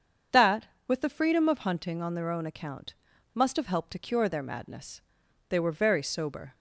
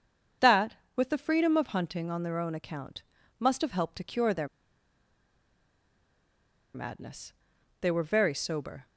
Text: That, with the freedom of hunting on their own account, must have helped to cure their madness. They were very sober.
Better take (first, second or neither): first